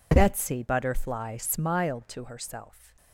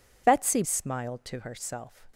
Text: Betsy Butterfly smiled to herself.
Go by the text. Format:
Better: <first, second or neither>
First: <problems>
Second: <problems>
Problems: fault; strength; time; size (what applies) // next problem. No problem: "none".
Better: first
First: none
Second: skips "Butterfly"; at 0.6 s